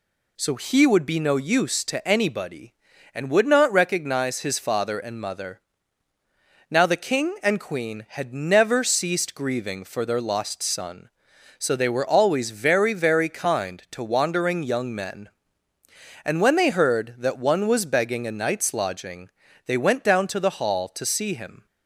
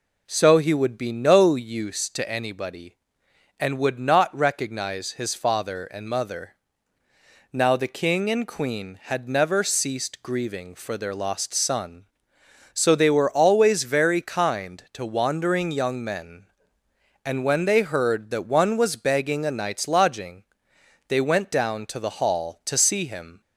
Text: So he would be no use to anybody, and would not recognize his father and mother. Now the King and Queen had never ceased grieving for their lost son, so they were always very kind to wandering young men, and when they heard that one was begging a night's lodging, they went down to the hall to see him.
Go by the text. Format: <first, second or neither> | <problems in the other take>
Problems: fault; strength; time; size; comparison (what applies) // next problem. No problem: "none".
second | says "very" twice; at 12.9 s